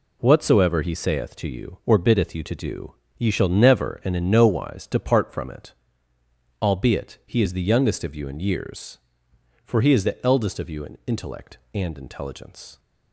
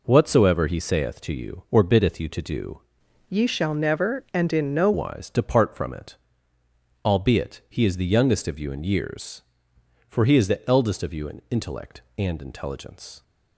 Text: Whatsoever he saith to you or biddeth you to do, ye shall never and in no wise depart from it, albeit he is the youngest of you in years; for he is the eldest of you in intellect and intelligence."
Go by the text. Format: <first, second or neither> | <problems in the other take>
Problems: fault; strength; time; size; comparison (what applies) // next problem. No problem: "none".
first | changes voice from "ye" to "no"; from 3.2 to 4.9 s; 1.7 s long